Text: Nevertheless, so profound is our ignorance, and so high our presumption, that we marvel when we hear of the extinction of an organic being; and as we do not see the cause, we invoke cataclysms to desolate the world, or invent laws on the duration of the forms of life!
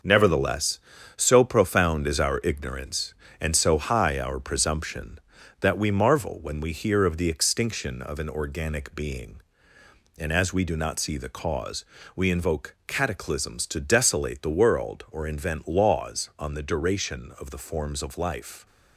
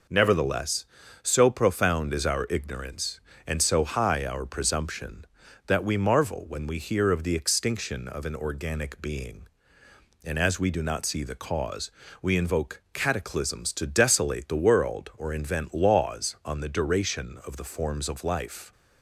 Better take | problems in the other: second | gets quieter; strong; throughout; 7.5 dB

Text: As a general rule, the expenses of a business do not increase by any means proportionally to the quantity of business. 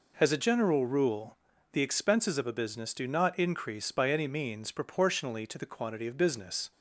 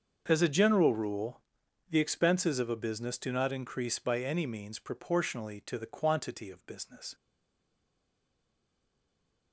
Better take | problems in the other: first | starts louder than the rest; until 1.2 s; 6.5 dB // stays silent after the last word; from 7.1 s on; 2.4 s long

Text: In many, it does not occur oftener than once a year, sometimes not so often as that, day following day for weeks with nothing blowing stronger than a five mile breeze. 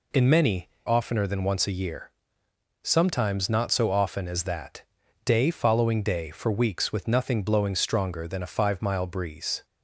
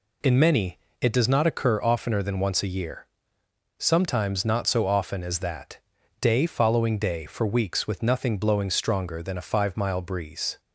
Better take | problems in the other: second | skips "it does not occur"; at 0.7 s

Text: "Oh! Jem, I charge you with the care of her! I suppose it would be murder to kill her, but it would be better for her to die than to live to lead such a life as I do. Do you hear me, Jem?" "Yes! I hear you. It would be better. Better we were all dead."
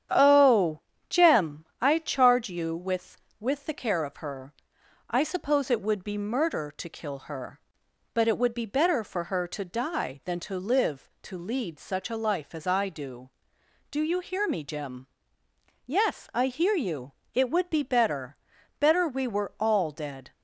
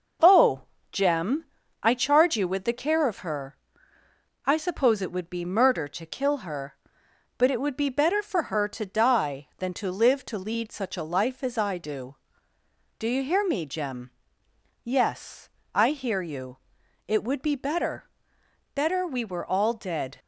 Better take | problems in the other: second | starts louder than the rest; strong; until 1.4 s; 9 dB // says "with" twice; at 3.3 s

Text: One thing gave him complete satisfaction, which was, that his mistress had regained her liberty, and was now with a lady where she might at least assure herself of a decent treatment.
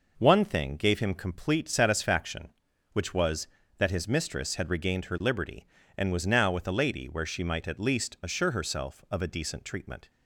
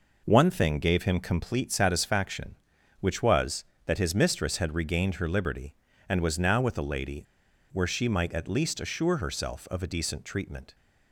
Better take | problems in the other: first | pauses between "lady" and "where"; noticeable; at 7.2 s; 0.50 s long

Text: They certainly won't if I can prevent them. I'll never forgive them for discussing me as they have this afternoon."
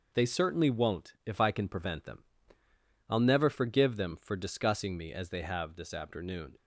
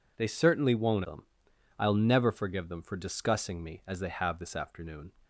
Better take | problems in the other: first | skips "if I can prevent"; at 1.0 s

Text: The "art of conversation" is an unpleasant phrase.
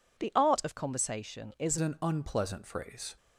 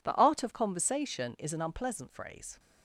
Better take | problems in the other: second | changes voice at "an"; from 1.7 s on; 1.4 s long

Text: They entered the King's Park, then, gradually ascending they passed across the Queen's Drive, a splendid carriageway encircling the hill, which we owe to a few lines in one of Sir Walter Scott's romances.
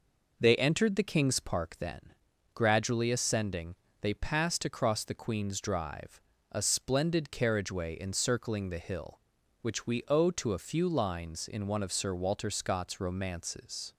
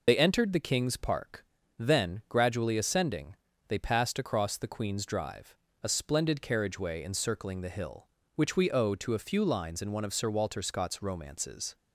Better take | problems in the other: first | loses the start of "They"; at 0.0 s; 70 ms // pauses between "ascending" and "they"; slight; at 3.3 s; 0.32 s long; slight in the first

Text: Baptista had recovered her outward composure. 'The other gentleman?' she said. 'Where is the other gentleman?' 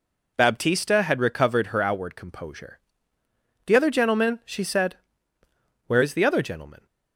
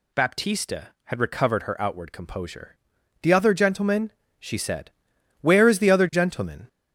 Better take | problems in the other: first | gets louder; noticeable; throughout; 4.5 dB

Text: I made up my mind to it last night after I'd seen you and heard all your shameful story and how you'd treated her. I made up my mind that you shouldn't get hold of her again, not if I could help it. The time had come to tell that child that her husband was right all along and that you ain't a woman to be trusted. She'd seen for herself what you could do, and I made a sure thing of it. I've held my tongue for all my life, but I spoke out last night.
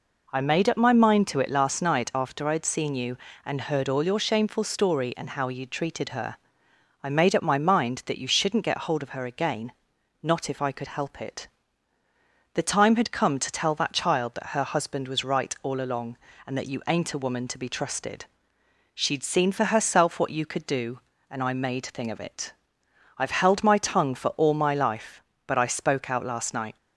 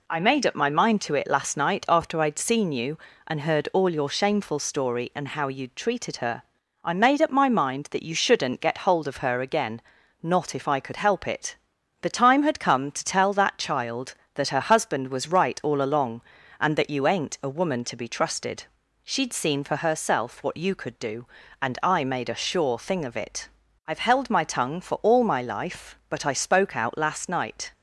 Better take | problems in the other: second | skips "a sure"; at 21.8 s

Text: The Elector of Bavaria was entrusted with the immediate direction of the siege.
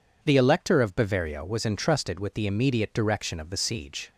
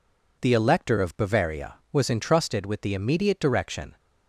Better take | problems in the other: first | stops before "of the siege"; at 3.9 s

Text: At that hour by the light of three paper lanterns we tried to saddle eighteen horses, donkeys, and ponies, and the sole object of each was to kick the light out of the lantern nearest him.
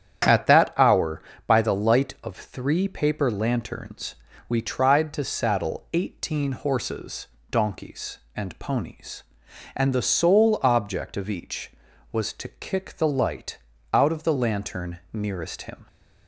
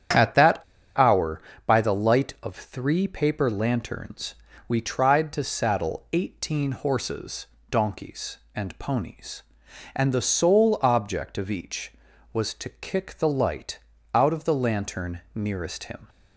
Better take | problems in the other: first | starts louder than the rest; strong; until 1.7 s; 9.5 dB; strong in the first // pauses between "that" and "hour"; slight; at 0.6 s; 0.35 s long // pauses between "lanterns" and "we"; slight; at 4.3 s; 0.32 s long; slight in the first // pauses between "light" and "out"; slight; at 13.7 s; 0.34 s long; slight in the first

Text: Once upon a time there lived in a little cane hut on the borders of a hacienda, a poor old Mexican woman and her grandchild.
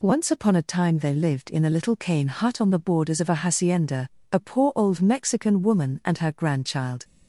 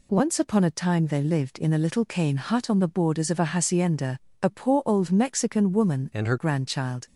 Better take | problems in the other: first | changes voice from "and" to "her"; from 6.1 to 6.3 s; 0.2 s long

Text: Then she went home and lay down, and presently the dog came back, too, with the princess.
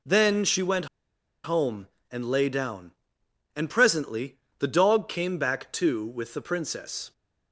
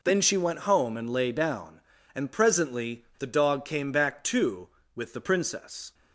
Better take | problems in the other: second | pauses between "went" and "home"; noticeable; at 0.8 s; 0.57 s long // pauses between "presently" and "the"; slight; at 4.3 s; 0.20 s long

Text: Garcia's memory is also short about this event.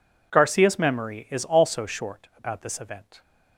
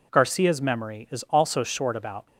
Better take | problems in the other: first | stops before "this event"; at 2.2 s

